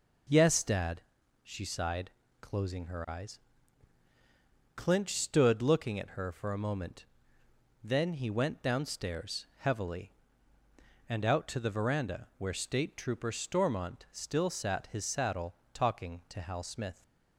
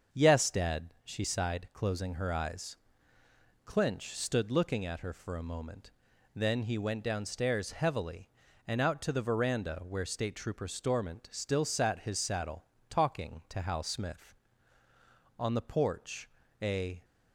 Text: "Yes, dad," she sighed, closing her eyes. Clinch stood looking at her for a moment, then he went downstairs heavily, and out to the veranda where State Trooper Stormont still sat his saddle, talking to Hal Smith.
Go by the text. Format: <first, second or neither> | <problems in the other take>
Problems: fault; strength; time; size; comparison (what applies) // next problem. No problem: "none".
first | starts louder than the rest; until 1.2 s; 6.5 dB // goes on to say "On the porch a"; from 15.3 s on; 1.6 s long